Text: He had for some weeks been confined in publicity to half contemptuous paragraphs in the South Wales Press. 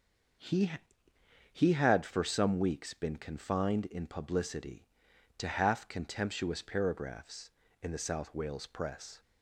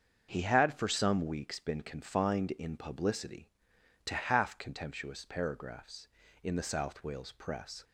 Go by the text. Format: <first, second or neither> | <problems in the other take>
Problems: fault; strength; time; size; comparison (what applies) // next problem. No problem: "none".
second | starts louder than the rest; until 2.2 s; 6 dB; also in the second // says "He" twice; at 1.5 s